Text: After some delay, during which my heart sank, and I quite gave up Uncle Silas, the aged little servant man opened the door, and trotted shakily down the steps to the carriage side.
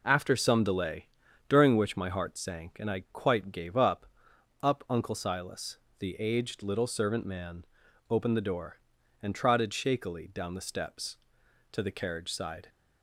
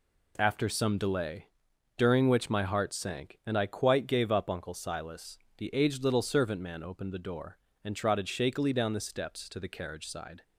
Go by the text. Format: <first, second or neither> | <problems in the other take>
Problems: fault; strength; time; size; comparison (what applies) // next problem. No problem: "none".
second | says "up" twice; at 4.6 s // pauses between "man" and "opened"; noticeable; at 7.6 s; 0.46 s long